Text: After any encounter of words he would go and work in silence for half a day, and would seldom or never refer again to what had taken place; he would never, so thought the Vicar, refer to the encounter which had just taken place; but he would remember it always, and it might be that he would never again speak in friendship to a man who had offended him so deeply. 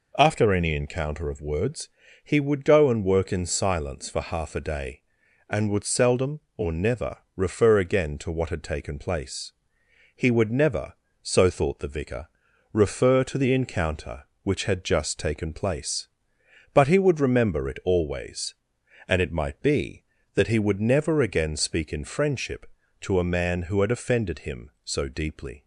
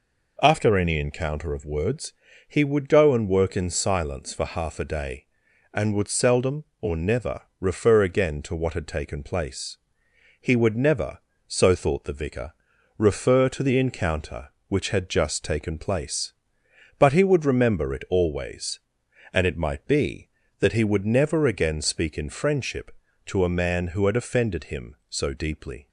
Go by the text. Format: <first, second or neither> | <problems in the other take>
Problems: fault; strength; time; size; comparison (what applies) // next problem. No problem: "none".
neither | pauses between "words" and "he"; the same in both // pauses between "never" and "refer"; slight; the same in both